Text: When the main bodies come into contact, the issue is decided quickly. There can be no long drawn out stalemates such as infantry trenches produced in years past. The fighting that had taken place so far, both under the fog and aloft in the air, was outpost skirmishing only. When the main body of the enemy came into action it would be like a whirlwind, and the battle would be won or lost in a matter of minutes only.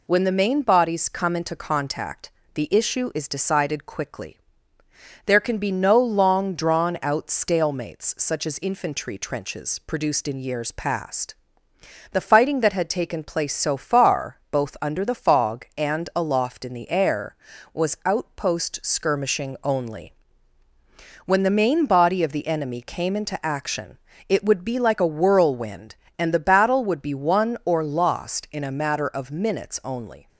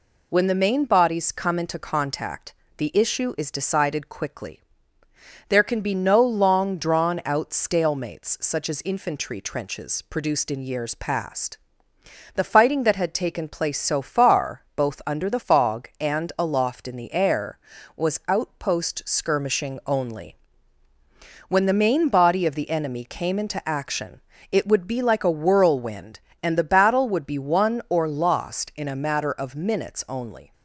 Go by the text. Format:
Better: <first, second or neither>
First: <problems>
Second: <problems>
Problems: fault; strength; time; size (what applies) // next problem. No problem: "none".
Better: neither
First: pauses between "action" and "it"; slight; at 23.9 s; 0.30 s long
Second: pauses between "action" and "it"; slight; at 24.2 s; 0.30 s long